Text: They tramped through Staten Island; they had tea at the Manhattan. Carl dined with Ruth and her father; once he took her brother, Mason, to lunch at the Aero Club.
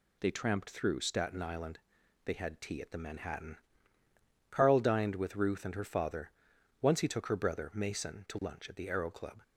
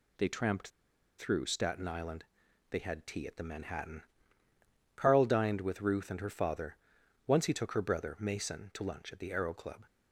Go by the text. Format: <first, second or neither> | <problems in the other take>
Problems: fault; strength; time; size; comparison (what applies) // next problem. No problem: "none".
first | pauses between "tramped" and "through"; noticeable; at 0.6 s; 0.50 s long